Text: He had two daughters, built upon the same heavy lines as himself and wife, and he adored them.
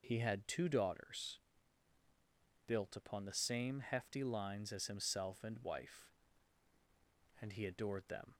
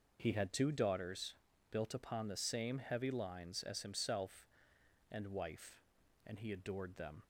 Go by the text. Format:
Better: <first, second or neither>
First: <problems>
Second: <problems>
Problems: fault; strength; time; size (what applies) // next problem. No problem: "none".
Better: second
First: says "hefty" for "heavy"; at 3.8 s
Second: none